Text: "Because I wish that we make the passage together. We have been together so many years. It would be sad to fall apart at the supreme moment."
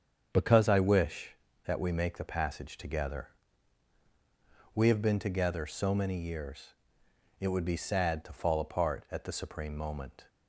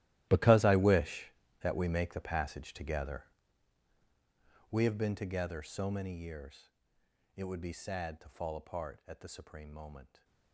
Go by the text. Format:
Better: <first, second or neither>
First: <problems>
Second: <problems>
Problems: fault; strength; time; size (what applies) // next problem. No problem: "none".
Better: first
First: starts louder than the rest; strong; until 1.3 s; 7.5 dB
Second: gets quieter; strong; throughout; 18 dB // starts louder than the rest; strong; until 1.3 s; 14.5 dB